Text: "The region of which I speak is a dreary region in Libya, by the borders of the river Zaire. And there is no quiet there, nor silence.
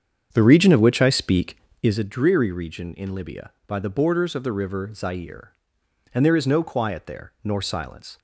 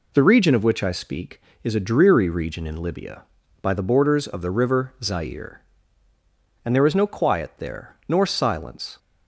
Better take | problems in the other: second | starts louder than the rest; strong; until 2.1 s; 7.5 dB

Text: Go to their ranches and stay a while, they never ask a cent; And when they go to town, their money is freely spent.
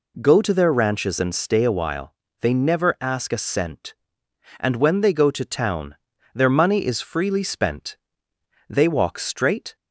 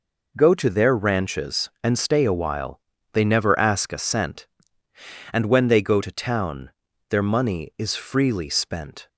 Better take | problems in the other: second | goes on to say "They walk straight"; noticeable; from 8.6 s on; 1.0 s long

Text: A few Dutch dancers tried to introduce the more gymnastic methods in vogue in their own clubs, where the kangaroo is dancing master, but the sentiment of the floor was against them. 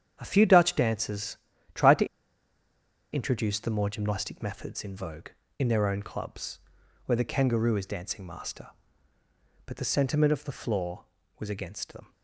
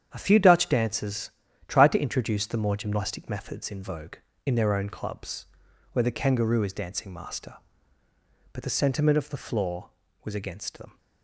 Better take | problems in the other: second | starts louder than the rest; strong; until 1.2 s; 9 dB; strong in the second // pauses between "dancers" and "tried"; at 1.3 s; 0.38 s long; also in the second // pauses between "to" and "introduce"; at 2.0 s; 1.0 s long

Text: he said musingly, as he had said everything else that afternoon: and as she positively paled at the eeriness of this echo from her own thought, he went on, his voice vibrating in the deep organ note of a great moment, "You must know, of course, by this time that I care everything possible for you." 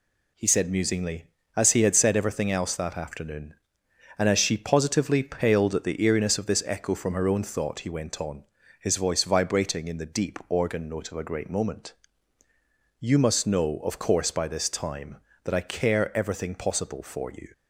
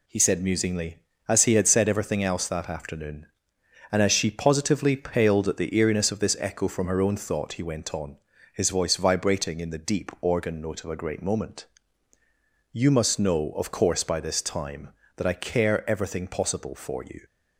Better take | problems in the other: neither | none

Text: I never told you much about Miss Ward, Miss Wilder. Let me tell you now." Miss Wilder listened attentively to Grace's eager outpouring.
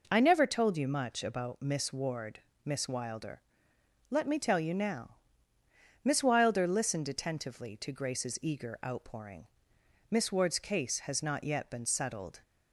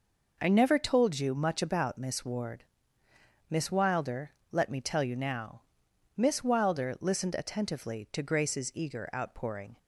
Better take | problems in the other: second | goes on to say "Miss Ward's case has not yet been settled"; strong; from 10.1 s on; 2.3 s long

